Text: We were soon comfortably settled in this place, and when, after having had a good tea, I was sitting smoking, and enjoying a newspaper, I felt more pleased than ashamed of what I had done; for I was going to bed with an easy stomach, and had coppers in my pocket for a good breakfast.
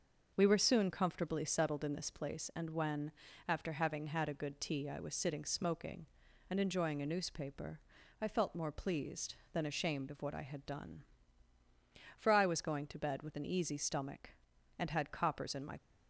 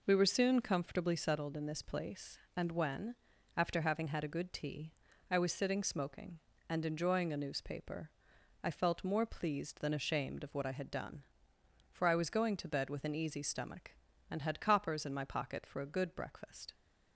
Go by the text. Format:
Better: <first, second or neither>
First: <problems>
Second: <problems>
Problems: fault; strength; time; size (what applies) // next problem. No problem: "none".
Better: second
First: starts louder than the rest; noticeable; until 1.3 s; 6 dB // stops before "pocket for a good breakfast"; at 15.7 s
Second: none